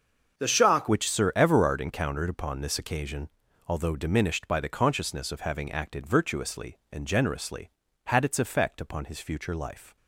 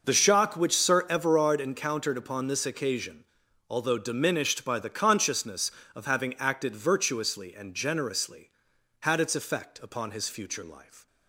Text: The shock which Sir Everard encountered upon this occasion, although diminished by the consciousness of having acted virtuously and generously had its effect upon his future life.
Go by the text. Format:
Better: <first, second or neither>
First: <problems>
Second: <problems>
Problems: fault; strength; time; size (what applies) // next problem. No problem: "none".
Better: second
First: starts louder than the rest; until 1.4 s; 6.5 dB // changes voice at "which"; from 0.8 s on; 9.1 s long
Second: none